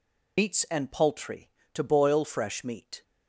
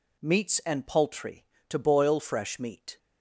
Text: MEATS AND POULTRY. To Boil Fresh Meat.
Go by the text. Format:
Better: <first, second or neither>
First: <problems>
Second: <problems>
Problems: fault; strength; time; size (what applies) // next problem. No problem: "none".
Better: second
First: loses the start of "MEATS"; at 0.3 s; 130 ms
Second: none